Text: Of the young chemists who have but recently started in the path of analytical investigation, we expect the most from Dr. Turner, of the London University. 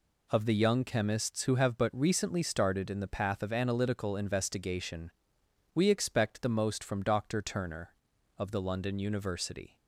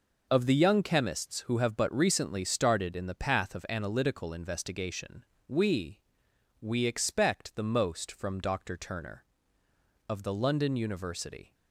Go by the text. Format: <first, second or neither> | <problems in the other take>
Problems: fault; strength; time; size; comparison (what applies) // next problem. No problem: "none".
first | says "we" twice; at 6.5 s